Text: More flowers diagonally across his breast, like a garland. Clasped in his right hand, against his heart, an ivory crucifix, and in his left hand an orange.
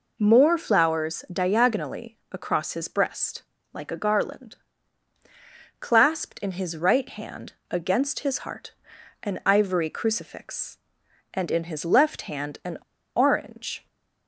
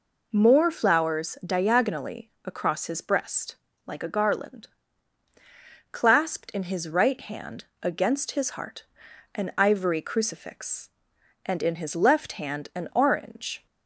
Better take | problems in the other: second | pauses between "diagonally" and "across"; slight; at 2.1 s; 0.16 s long; slight in the second // pauses between "an" and "orange"; at 12.7 s; 0.38 s long

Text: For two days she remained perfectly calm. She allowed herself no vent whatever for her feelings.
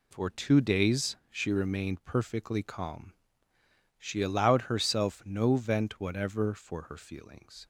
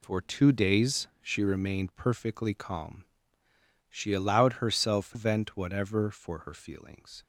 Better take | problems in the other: first | skips "no"; at 5.1 s

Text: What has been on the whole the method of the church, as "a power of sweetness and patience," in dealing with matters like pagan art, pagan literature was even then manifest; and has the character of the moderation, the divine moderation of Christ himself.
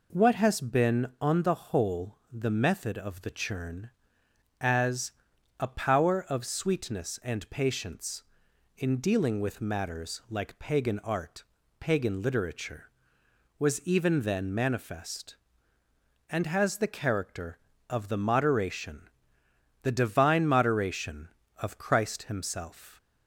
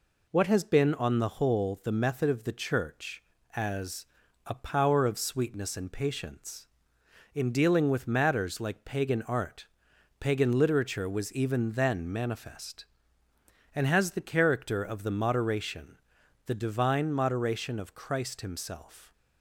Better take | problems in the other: second | says "churn" for "church"; at 3.3 s // pauses between "as" and "a"; noticeable; at 5.1 s; 0.48 s long; also in the second

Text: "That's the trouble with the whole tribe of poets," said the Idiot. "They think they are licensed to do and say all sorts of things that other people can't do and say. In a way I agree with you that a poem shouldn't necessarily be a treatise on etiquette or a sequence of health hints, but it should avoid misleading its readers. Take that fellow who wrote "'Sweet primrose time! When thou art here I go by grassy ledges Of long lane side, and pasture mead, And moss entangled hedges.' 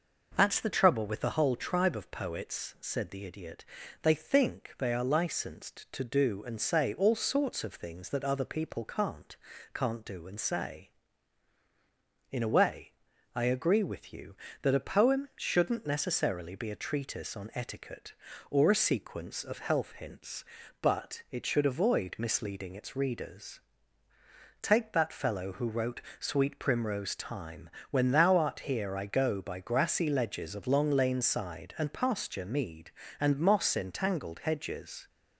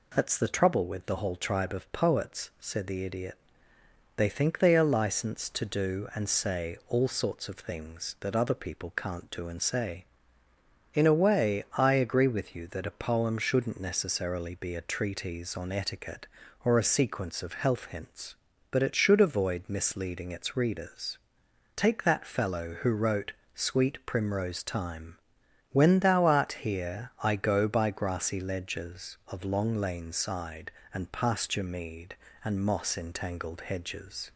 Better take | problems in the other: second | says "can't" twice; at 9.7 s // pauses between "way" and "I"; at 12.9 s; 0.42 s long // pauses between "wrote" and "Sweet"; slight; at 26.0 s; 0.20 s long; slight in the second

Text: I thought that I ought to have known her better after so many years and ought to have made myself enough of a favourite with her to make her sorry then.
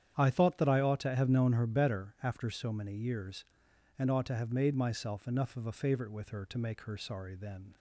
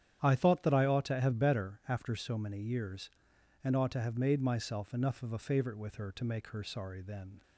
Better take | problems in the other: first | starts louder than the rest; strong; until 1.2 s; 10 dB; strong in the first // skips "known her"; at 1.3 s

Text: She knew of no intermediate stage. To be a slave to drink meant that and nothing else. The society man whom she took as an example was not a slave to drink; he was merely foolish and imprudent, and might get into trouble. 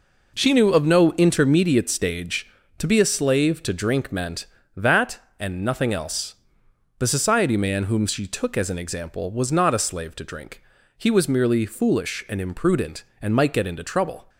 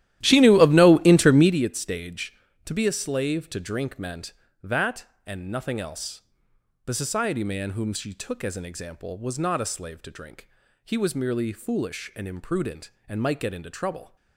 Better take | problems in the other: first | starts louder than the rest; strong; until 1.6 s; 13 dB

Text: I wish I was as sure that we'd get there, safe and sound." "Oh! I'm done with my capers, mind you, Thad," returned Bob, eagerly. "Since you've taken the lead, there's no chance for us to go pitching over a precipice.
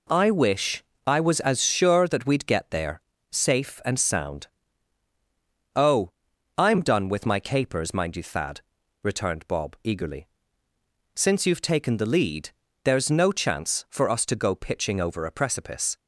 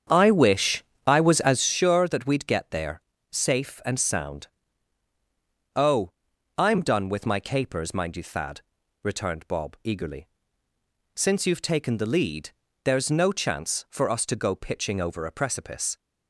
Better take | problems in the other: first | starts louder than the rest; strong; until 1.6 s; 8 dB // pauses between "wish" and "I"; slight; at 0.8 s; 0.24 s long; slight in the first

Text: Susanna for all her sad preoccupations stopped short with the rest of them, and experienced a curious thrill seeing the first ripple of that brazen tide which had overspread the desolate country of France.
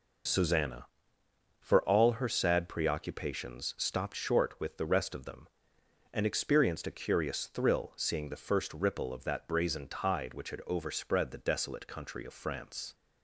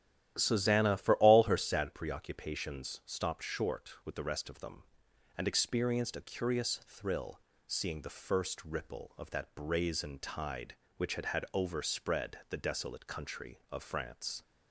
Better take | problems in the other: first | starts louder than the rest; strong; until 1.3 s; 12 dB // pauses between "thrill" and "seeing"; slight; at 7.3 s; 0.28 s long // says "had" twice; at 11.2 s

